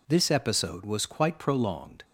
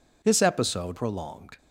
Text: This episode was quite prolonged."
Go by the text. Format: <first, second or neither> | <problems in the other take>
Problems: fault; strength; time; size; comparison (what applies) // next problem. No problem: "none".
first | skips "was quite"; at 0.9 s